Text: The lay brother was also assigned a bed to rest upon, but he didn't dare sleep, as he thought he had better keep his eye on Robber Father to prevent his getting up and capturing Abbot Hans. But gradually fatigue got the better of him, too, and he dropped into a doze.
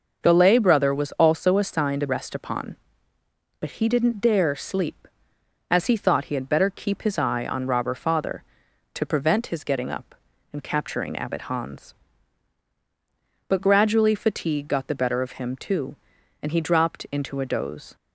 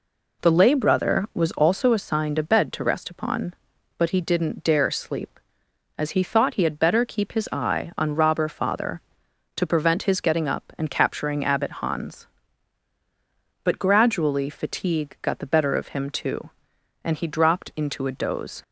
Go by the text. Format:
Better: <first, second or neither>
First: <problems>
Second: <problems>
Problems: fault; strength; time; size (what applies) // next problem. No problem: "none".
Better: second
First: starts louder than the rest; noticeable; until 1.2 s; 6 dB // skips "bed to"; at 2.0 s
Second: none